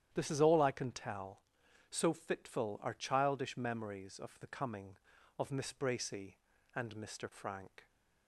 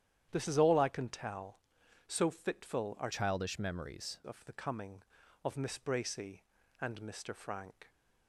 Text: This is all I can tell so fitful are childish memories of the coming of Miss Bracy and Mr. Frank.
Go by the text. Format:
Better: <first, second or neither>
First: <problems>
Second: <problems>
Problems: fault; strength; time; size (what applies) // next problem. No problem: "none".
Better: first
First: starts louder than the rest; strong; until 1.1 s; 10.5 dB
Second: starts louder than the rest; strong; until 1.3 s; 10 dB // changes voice from "childish" to "memories"; from 3.1 to 4.1 s; 1.0 s long